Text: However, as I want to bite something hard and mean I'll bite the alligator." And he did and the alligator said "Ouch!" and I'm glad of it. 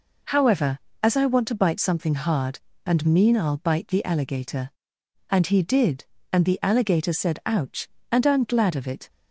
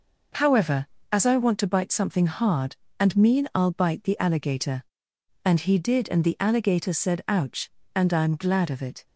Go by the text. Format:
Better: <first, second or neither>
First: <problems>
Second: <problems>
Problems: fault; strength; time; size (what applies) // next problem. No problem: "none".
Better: neither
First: none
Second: none